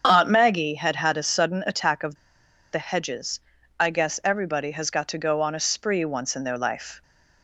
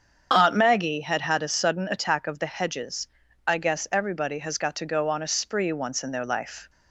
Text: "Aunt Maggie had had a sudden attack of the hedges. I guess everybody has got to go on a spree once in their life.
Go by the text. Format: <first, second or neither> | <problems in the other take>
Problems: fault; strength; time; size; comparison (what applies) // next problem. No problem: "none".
second | starts louder than the rest; strong; until 1.0 s; 7.5 dB; strong in the second // pauses between "of" and "the"; noticeable; at 2.1 s; 0.58 s long